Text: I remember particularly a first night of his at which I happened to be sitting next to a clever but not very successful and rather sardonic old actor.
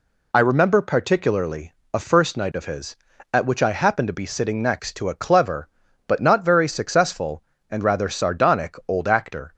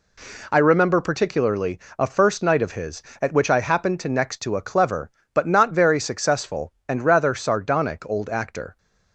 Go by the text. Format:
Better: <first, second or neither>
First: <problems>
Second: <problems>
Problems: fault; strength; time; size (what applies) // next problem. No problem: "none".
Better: first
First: pauses between "particularly" and "a"; slight; at 1.7 s; 0.22 s long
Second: pauses between "particularly" and "a"; slight; at 1.7 s; 0.18 s long // skips "be sitting"; at 4.0 s